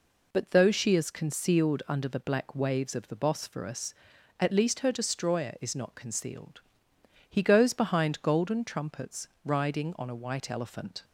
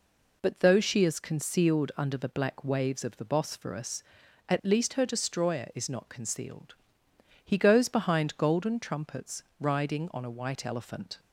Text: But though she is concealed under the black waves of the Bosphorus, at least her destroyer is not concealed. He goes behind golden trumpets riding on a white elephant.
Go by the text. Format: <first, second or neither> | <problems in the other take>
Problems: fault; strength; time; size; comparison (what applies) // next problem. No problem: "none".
neither | pauses between "trumpets" and "riding"; slight; the same in both